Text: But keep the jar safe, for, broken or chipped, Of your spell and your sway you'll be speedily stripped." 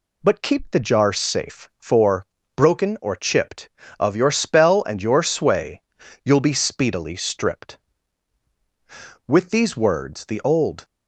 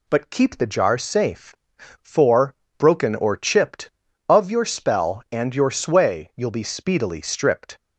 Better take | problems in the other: second | pauses between "sway" and "you'll"; noticeable; at 5.8 s; 0.46 s long // goes on to say "With these words the old"; from 9.2 s on; 1.5 s long

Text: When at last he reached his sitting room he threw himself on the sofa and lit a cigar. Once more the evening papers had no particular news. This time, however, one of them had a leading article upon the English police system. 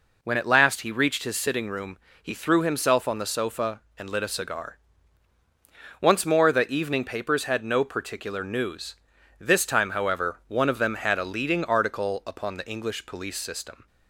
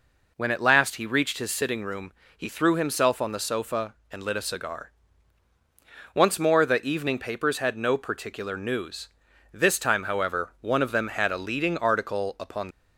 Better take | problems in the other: first | pauses between "room" and "he"; slight; at 2.1 s; 0.24 s long; slight in the first // stops before "the English police system"; at 12.7 s

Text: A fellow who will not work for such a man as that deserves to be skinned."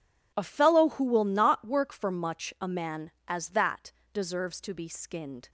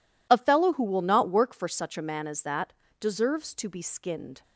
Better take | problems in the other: second | says "much" for "such"; at 2.1 s // pauses between "that" and "deserves"; slight; at 3.9 s; 0.22 s long; slight in the second

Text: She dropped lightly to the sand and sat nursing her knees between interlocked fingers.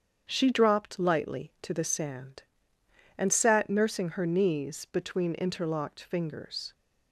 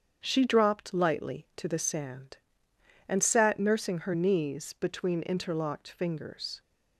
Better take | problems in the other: neither | starts louder than the rest; strong; the same in both

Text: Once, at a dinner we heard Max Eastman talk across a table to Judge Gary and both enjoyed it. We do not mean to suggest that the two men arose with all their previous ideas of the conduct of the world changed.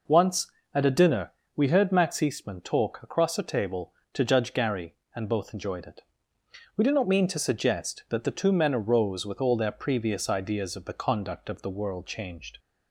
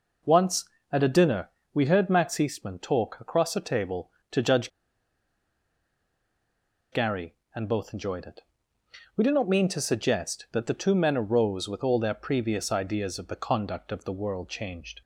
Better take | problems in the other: first | pauses between "dinner" and "we"; slight; at 1.4 s; 0.24 s long; slight in the first // pauses between "Judge" and "Gary"; strong; at 4.7 s; 2.2 s long

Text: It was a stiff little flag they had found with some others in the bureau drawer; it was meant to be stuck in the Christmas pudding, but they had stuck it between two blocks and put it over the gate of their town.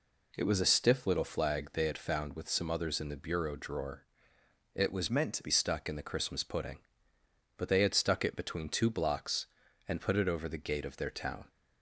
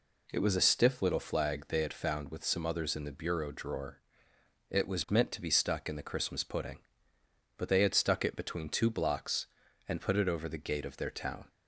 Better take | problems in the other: second | changes voice from "meant" to "be"; from 5.0 to 5.5 s; 0.5 s long

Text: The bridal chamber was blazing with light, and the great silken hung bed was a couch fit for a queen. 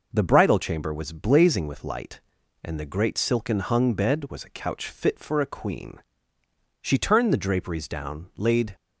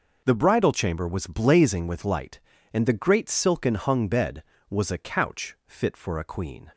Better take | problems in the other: second | goes on to say "She turned the draperies down laid"; strong; from 6.8 s on; 1.9 s long

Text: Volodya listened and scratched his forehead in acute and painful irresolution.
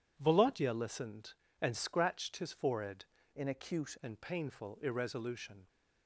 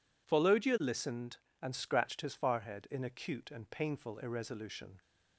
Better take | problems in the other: second | changes voice from "in" to "acute"; from 3.3 to 3.9 s; 0.6 s long

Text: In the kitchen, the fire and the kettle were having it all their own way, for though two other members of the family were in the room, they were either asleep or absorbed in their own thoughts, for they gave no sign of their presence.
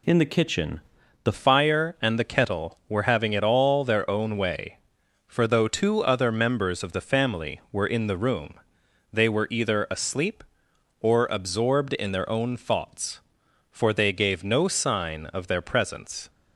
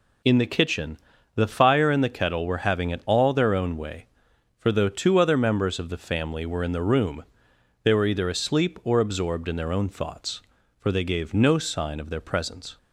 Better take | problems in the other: second | changes voice at "fire"; from 1.3 s on; 14.9 s long

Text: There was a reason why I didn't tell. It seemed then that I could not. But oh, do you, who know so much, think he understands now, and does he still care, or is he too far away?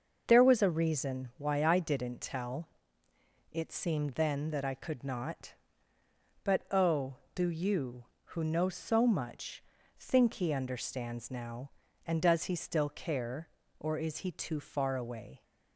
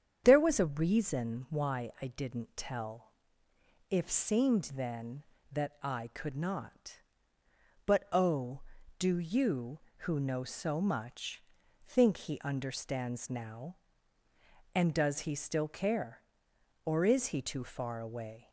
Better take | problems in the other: first | starts louder than the rest; strong; until 1.2 s; 8 dB; noticeable in the first // says "If" for "It"; at 3.9 s

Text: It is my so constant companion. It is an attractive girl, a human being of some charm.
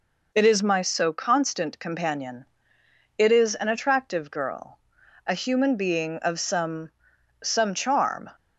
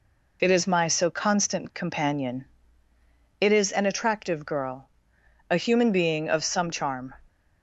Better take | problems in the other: second | says "some" twice; at 7.4 s

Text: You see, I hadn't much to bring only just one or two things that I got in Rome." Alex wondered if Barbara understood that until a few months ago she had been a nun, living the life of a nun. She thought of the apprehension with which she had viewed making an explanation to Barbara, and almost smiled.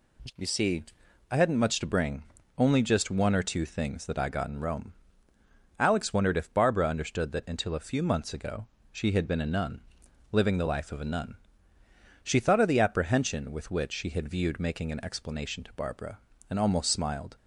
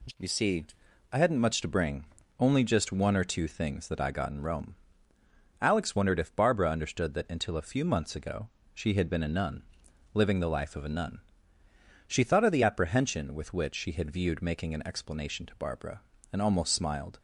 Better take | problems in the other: neither | pauses between "bring" and "only"; slight; the same in both // pauses between "ago" and "she"; slight; the same in both

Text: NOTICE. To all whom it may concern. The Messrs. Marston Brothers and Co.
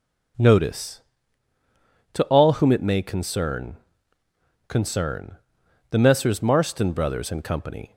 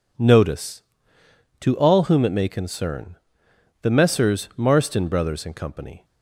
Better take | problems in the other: second | says "concern" twice; at 4.6 s

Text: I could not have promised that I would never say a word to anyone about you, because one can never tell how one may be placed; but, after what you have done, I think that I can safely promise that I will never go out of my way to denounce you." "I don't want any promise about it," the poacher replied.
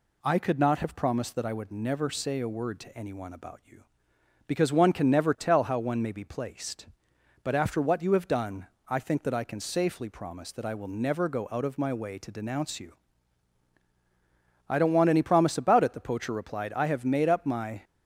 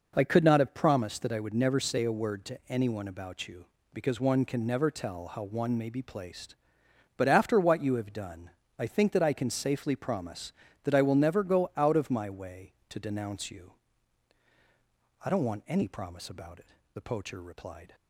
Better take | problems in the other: second | goes on to say "I have made up my"; noticeable; from 16.7 s on; 1.0 s long

